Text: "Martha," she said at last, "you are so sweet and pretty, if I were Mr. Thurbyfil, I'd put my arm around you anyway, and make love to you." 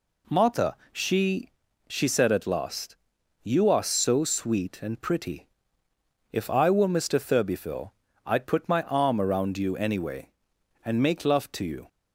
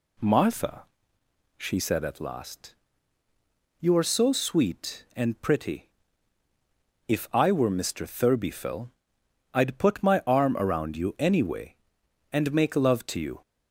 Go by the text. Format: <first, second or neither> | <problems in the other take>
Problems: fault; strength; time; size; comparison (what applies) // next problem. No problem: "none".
second | says "she" twice; at 1.8 s